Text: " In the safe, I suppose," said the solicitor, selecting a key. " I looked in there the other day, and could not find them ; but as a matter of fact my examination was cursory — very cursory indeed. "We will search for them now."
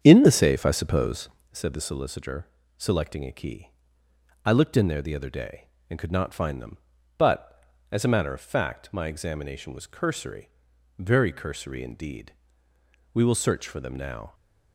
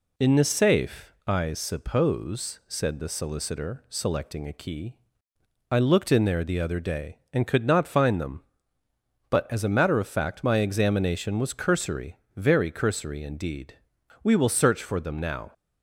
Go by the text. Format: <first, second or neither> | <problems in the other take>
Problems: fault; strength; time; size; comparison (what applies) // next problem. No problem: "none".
second | starts louder than the rest; strong; until 1.6 s; 8.5 dB